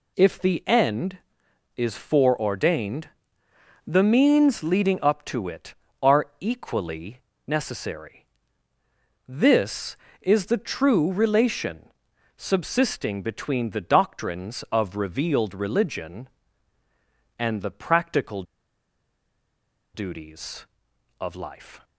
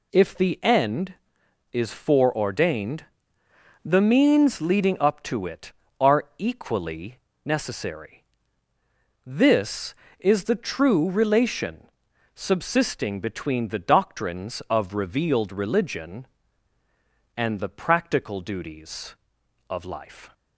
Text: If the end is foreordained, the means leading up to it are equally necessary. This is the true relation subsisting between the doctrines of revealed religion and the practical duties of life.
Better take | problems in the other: second | pauses between "equally" and "necessary"; slight; at 7.1 s; 0.28 s long; slight in the second // pauses between "relation" and "subsisting"; noticeable; at 11.8 s; 0.48 s long; noticeable in the second // pauses between "practical" and "duties"; strong; at 18.4 s; 1.5 s long

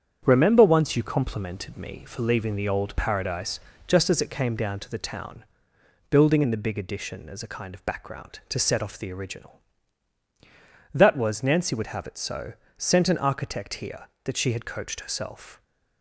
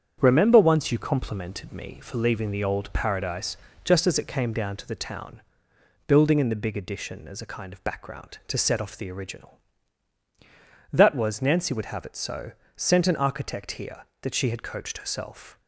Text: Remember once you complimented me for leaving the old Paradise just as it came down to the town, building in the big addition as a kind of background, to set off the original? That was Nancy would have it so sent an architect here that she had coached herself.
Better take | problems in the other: neither | starts louder than the rest; strong; the same in both // pauses between "Paradise" and "just"; slight; the same in both // pauses between "so" and "sent"; slight; the same in both

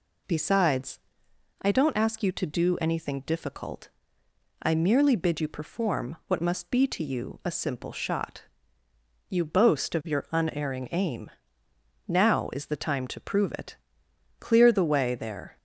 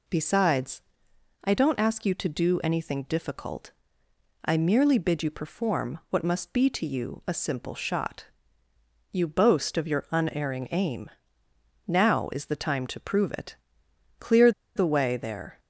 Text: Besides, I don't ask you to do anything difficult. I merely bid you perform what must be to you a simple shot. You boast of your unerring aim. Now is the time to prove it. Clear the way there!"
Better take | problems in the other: first | pauses between "Clear" and "the"; slight; at 14.5 s; 0.25 s long

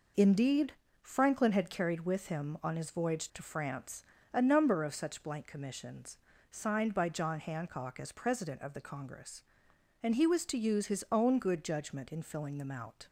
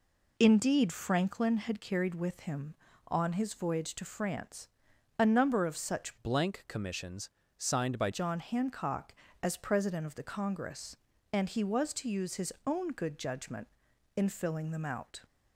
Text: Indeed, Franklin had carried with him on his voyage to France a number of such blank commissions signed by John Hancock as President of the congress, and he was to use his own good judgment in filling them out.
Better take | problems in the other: first | pauses between "France" and "a"; noticeable; at 4.6 s; 0.50 s long; slight in the first // changes voice from "blank" to "by"; from 6.2 to 8.0 s; 1.8 s long // pauses between "commissions" and "signed"; slight; at 7.2 s; 0.28 s long; slight in the first

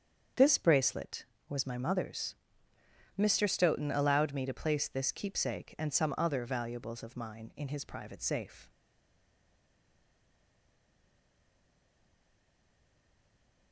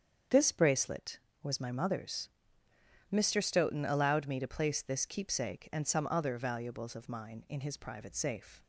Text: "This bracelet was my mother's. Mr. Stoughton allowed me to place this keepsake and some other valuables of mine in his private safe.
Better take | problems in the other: second | starts louder than the rest; strong; until 1.6 s; 7.5 dB; strong in the second // stays silent after the last word; strong; from 8.6 s on; 5.1 s long

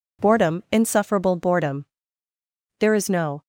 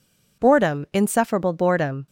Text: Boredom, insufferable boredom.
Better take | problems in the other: second | goes on to say "There is no"; noticeable; from 2.7 s on; 0.62 s long

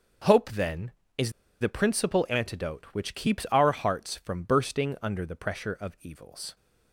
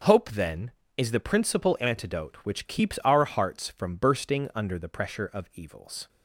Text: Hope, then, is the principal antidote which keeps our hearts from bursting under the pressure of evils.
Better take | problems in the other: second | starts louder than the rest; until 1.7 s; 6 dB; also in the second // pauses between "is" and "the"; slight; at 1.3 s; 0.29 s long

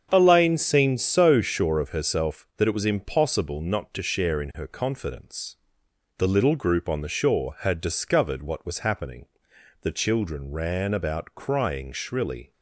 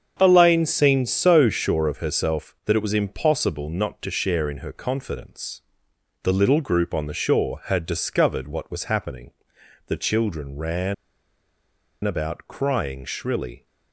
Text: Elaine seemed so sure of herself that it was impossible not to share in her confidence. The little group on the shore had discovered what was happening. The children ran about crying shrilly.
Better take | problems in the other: first | starts louder than the rest; strong; until 1.2 s; 7.5 dB; strong in the first // pauses between "ran" and "about"; at 10.9 s; 1.1 s long

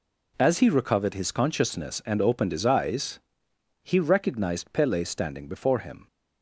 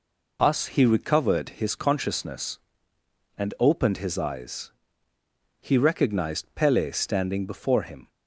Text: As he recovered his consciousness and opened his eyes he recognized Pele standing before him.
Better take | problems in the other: first | says "Us" for "As"; at 0.4 s // pauses between "eyes" and "he"; noticeable; at 4.7 s; 0.90 s long; noticeable in the first

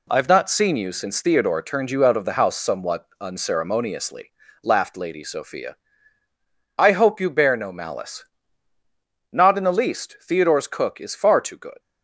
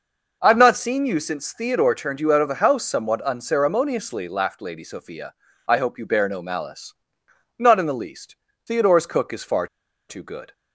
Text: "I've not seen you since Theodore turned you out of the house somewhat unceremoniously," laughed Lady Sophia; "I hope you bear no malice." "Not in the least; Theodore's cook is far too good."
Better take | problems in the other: first | pauses between "far" and "too"; at 9.6 s; 0.41 s long

